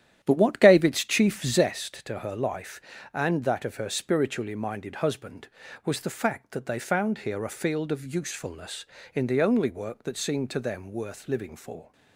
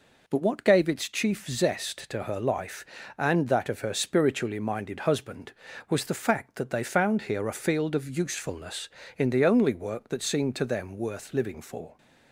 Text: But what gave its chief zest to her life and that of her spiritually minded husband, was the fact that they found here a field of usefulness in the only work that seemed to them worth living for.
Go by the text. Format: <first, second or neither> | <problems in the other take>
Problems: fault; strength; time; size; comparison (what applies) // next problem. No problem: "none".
second | starts louder than the rest; strong; until 1.8 s; 11 dB